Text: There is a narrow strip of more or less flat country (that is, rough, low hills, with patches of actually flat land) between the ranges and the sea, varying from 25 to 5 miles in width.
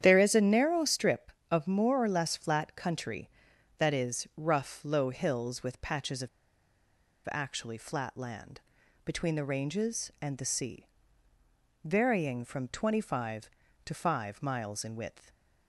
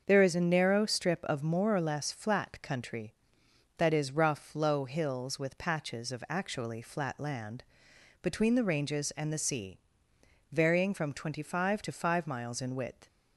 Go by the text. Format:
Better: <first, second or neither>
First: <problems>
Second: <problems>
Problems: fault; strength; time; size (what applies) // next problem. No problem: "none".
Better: second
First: starts louder than the rest; strong; until 1.0 s; 9.5 dB // pauses between "of" and "actually"; at 6.2 s; 1.0 s long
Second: starts louder than the rest; until 1.0 s; 6.5 dB